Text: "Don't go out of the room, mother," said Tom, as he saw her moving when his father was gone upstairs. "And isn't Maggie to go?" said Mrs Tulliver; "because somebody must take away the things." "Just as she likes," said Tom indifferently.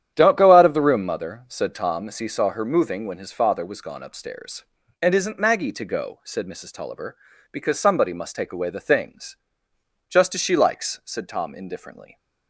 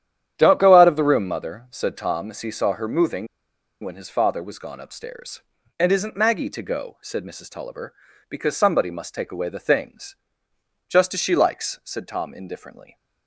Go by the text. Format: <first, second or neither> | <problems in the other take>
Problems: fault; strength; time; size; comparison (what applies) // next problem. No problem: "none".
first | starts louder than the rest; strong; until 1.3 s; 10 dB; strong in the first // pauses between "moving" and "when"; noticeable; at 3.2 s; 0.57 s long